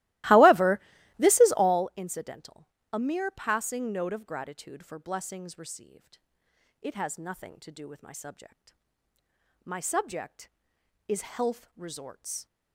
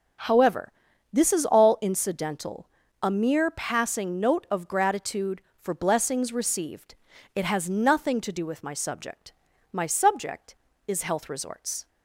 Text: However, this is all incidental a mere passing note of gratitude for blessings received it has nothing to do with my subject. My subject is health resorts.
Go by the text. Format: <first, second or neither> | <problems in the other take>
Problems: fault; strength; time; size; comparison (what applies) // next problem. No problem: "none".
second | starts louder than the rest; strong; until 1.9 s; 18 dB // pauses between "incidental" and "a"; slight; at 2.6 s; 0.24 s long; slight in the second // pauses between "received" and "it"; noticeable; at 6.1 s; 0.64 s long; also in the second